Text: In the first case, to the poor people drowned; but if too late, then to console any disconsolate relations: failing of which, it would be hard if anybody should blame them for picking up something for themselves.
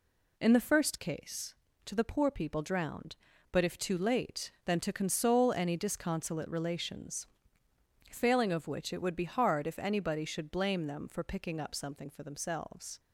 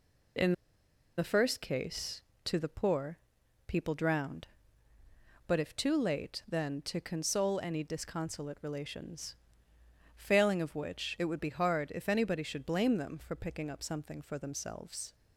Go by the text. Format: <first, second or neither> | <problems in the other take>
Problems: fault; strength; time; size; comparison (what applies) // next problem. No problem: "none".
first | pauses between "In" and "the"; noticeable; at 0.5 s; 0.64 s long // pauses between "poor" and "people"; noticeable; at 3.1 s; 0.52 s long